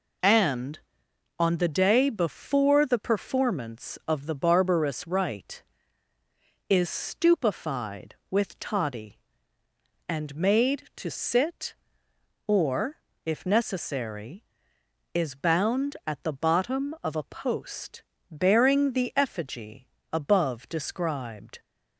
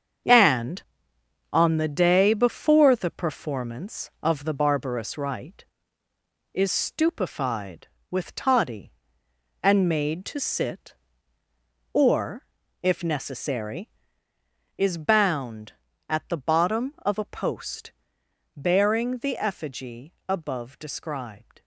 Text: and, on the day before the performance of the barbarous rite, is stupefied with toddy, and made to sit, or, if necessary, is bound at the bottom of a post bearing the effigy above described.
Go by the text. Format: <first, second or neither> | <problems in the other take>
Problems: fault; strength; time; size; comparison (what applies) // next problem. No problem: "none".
first | gets quieter; strong; throughout; 9 dB // pauses between "post" and "bearing"; noticeable; at 17.9 s; 0.64 s long; slight in the first // pauses between "effigy" and "above"; slight; at 20.1 s; 0.16 s long; slight in the first